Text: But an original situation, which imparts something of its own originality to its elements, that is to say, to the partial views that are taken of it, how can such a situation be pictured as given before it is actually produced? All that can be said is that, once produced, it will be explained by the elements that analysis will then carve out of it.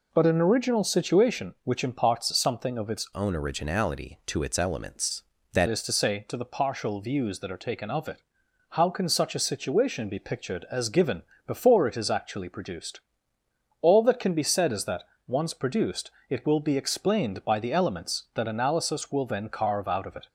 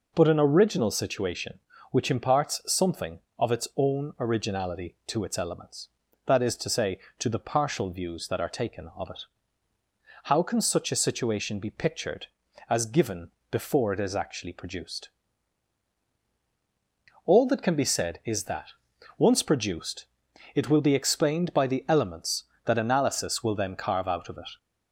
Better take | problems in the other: second | changes voice from "own" to "that"; from 3.1 to 5.6 s; 2.5 s long // pauses between "given" and "before"; slight; at 11.2 s; 0.24 s long; slight in the second

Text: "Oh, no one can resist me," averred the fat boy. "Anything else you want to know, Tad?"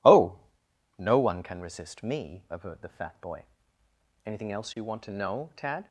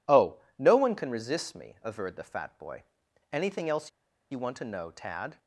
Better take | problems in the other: first | pauses between "else" and "you"; at 3.8 s; 0.42 s long

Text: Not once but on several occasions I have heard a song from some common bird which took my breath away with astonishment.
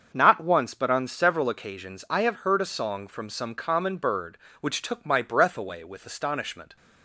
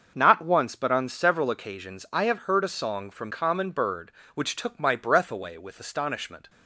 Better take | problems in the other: first | starts louder than the rest; until 1.1 s; 6.5 dB; also in the first // skips "some"; at 3.3 s

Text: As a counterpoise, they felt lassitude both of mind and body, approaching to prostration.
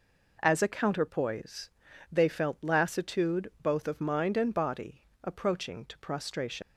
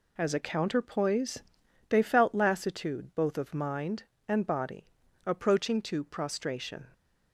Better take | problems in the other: second | leaves "prostration" unfinished; at 6.6 s; 65 ms

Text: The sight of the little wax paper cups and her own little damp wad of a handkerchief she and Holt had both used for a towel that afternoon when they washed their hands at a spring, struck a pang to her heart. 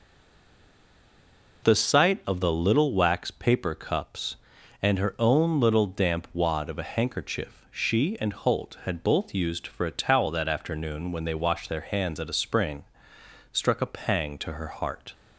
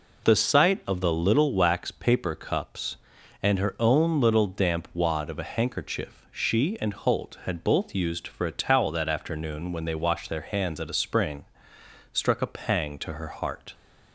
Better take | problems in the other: second | stays silent before the first word; noticeable; until 1.6 s; 1.6 s long

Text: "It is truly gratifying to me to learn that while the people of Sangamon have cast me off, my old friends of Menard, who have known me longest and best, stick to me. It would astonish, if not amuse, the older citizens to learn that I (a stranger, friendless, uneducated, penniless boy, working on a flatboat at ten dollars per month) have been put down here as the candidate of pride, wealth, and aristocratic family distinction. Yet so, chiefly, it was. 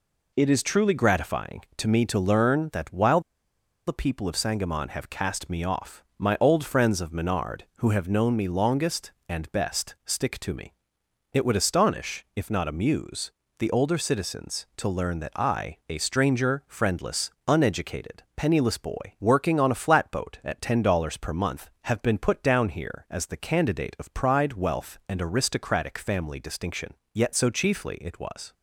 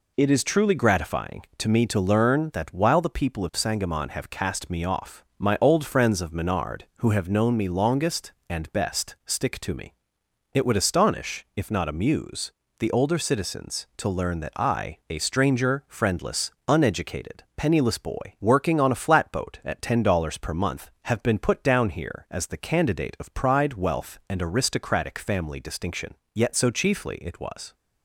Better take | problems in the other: second | pauses between "while" and "the"; noticeable; at 3.2 s; 0.65 s long

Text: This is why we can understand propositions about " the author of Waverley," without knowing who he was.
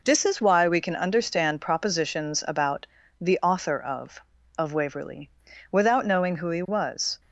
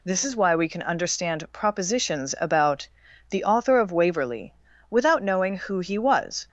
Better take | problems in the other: second | says "of" twice; at 4.5 s

